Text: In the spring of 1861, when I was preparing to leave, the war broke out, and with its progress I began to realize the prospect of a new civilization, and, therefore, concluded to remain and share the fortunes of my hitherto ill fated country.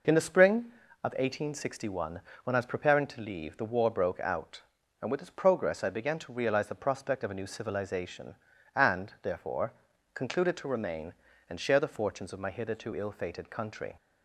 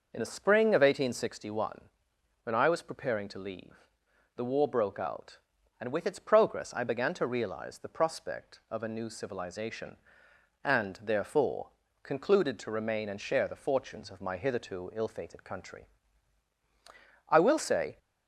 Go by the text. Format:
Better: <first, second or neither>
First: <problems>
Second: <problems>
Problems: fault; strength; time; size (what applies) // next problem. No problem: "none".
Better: first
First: none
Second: goes on to say "I will say"; noticeable; from 17.2 s on; 0.70 s long